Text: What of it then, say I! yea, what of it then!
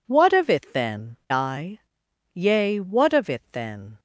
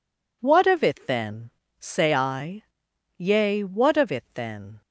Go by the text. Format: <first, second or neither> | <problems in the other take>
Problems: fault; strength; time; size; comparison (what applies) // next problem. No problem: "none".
second | skips "say"; at 1.2 s